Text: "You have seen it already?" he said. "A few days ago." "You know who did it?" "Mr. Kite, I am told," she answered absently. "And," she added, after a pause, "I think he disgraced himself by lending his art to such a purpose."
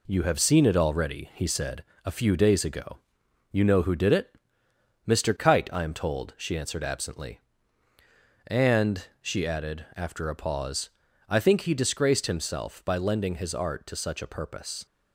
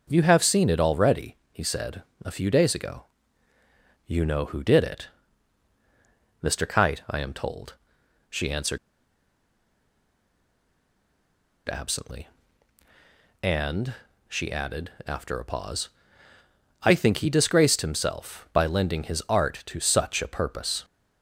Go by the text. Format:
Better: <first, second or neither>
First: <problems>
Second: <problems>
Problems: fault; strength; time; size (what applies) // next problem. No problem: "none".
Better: first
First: none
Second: pauses between "answered" and "absently"; strong; at 8.7 s; 2.9 s long